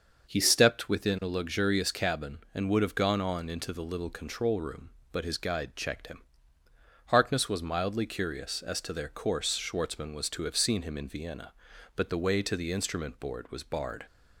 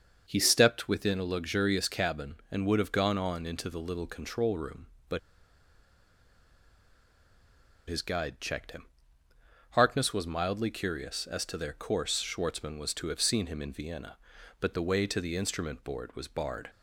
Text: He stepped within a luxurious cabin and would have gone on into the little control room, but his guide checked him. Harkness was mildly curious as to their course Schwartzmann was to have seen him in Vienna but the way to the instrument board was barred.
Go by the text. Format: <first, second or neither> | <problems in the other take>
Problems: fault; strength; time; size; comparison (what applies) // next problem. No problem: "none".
first | starts louder than the rest; until 1.2 s; 6 dB; also in the first // pauses between "but" and "his"; strong; at 5.1 s; 2.6 s long